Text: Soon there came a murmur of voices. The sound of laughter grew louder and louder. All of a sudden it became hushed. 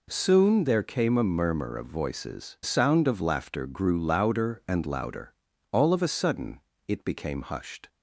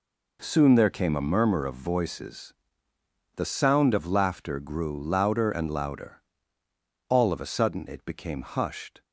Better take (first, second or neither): second